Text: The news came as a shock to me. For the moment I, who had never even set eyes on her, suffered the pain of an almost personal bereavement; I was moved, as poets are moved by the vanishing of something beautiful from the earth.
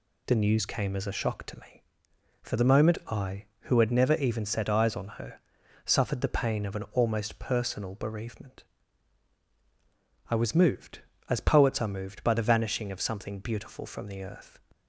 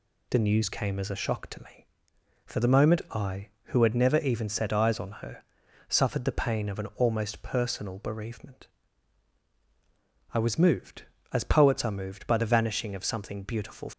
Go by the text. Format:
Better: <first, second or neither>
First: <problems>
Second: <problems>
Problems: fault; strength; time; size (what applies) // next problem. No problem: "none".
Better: first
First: none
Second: stops before "from the earth"; at 13.9 s